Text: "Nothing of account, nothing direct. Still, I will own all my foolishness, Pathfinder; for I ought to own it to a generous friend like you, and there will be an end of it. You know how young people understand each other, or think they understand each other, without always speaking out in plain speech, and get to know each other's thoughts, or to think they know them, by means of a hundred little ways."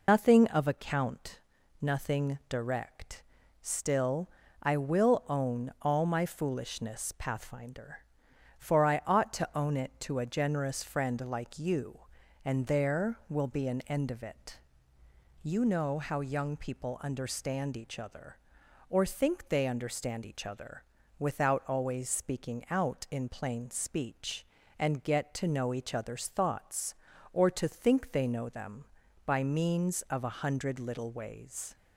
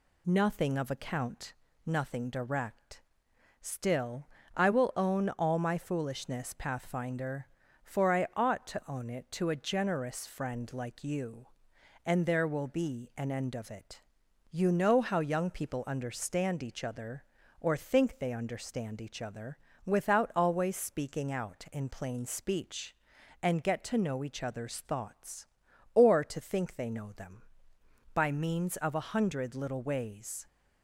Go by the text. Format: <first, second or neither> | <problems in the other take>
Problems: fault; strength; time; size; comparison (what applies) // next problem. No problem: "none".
second | loses the start of "Nothing"; at 0.0 s; 115 ms